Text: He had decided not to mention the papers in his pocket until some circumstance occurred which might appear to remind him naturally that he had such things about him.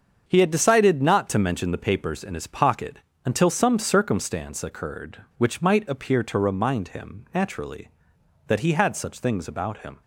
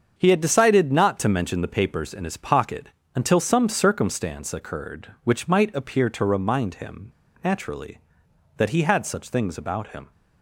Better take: first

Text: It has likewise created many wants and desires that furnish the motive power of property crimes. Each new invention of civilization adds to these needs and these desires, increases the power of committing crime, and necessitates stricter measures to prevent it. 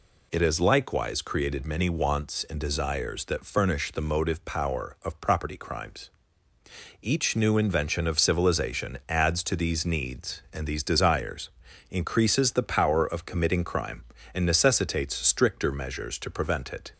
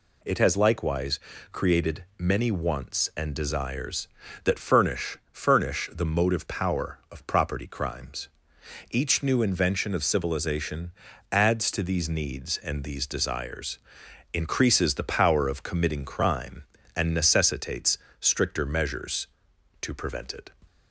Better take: first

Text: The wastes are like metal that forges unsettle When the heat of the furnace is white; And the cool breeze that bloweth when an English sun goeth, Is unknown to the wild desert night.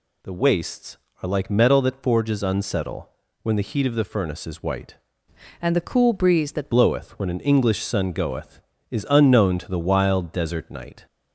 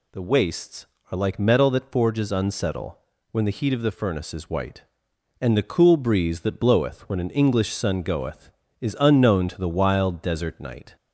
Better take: second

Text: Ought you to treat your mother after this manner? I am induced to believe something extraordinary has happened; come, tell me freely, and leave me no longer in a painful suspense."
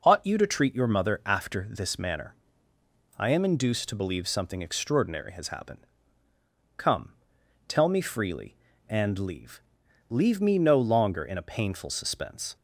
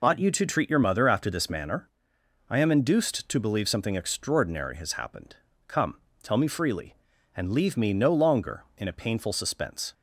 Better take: second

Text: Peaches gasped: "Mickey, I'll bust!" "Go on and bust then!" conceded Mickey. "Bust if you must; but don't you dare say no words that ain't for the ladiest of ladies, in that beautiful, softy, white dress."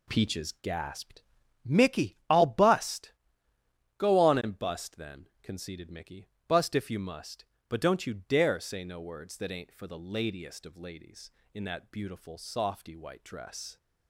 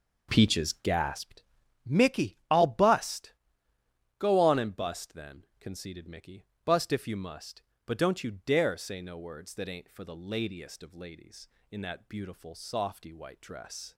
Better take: first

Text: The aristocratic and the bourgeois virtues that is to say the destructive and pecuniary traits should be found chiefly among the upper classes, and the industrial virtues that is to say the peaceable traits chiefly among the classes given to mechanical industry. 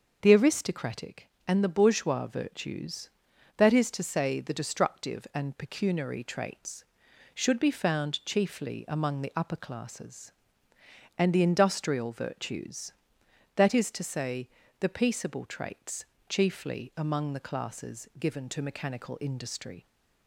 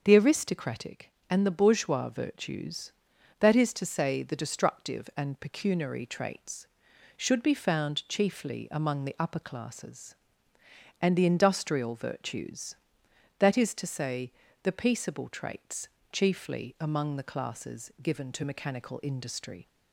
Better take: neither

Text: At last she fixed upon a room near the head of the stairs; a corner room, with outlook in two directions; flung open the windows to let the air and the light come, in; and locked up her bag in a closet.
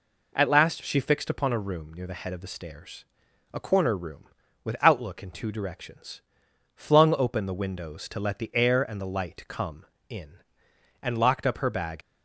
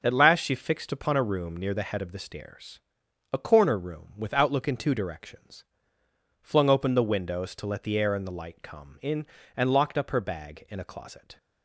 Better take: second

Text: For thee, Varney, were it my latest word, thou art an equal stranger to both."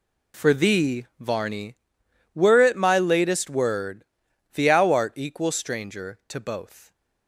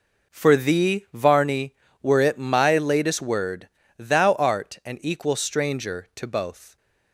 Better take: second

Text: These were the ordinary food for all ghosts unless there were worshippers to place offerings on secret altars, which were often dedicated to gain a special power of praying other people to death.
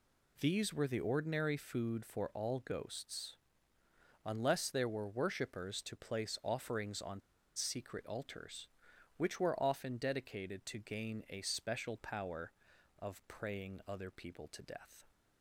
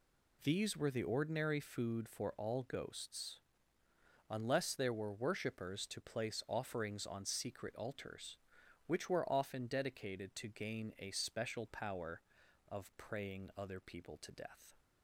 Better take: second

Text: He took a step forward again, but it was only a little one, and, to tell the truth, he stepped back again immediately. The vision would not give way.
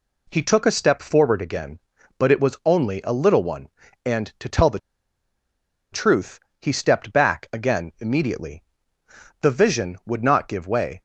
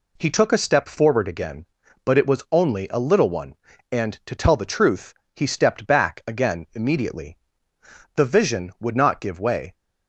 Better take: second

